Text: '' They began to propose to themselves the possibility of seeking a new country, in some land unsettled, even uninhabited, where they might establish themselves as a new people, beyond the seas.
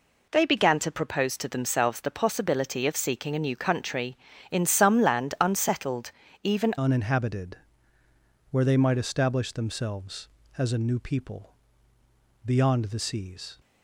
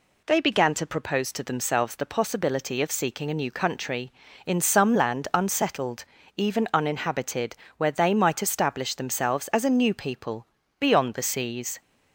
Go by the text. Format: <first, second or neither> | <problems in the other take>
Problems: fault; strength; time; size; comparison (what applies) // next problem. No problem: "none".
second | changes voice at "uninhabited"; from 6.7 s on; 6.8 s long